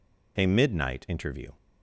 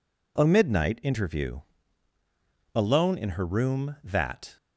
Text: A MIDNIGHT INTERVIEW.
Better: first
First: none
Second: goes on to say "Alone in her room that"; strong; from 2.7 s on; 1.8 s long

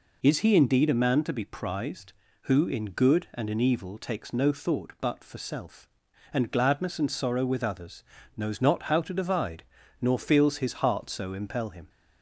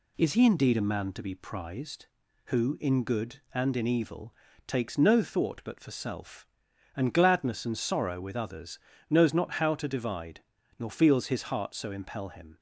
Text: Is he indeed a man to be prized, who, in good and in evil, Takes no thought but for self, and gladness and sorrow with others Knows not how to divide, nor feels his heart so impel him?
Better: neither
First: pauses between "others" and "Knows"; slight; at 8.0 s; 0.32 s long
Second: pauses between "others" and "Knows"; slight; at 8.7 s; 0.32 s long

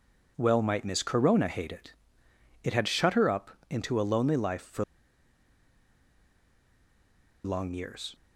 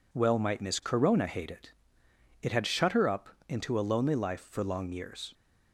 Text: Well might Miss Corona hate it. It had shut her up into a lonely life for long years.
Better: second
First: pauses between "up" and "into"; slight; at 3.5 s; 0.20 s long // pauses between "for" and "long"; strong; at 4.8 s; 2.6 s long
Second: pauses between "up" and "into"; slight; at 3.2 s; 0.20 s long

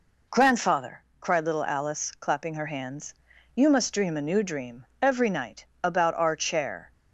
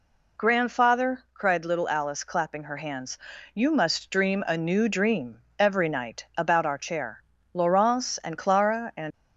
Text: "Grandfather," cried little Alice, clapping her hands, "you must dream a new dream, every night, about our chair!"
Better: first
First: none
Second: goes on to say "Laurence and Clara and"; from 7.5 s on; 1.6 s long

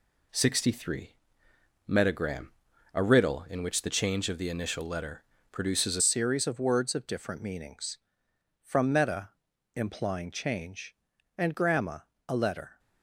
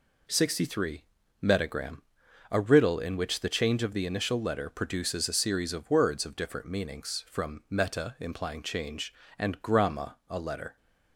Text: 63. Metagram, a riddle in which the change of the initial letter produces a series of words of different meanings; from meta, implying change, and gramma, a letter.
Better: second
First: pauses between "letter" and "produces"; slight; at 5.2 s; 0.28 s long // changes voice at "series"; from 6.0 s on; 6.7 s long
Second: none

